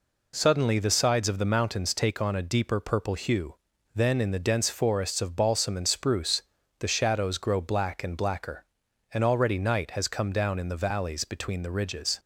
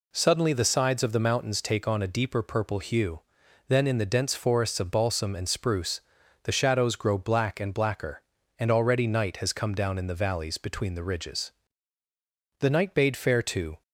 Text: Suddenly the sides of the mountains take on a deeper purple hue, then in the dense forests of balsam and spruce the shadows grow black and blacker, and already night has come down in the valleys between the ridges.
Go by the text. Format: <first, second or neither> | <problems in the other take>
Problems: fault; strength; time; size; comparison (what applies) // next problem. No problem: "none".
first | pauses between "spruce" and "the"; at 6.0 s; 0.42 s long; also in the first // goes on to say "The night bade fair to"; noticeable; from 12.5 s on; 1.2 s long